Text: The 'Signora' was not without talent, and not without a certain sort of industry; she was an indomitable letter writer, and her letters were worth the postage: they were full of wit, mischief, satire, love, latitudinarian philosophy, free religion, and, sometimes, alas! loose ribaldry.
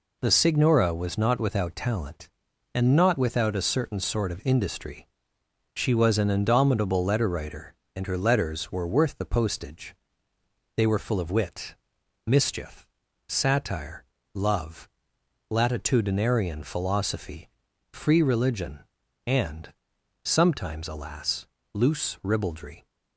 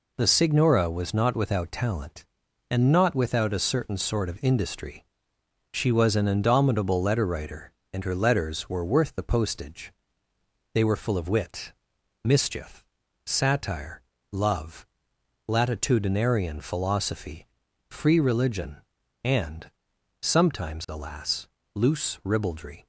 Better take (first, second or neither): neither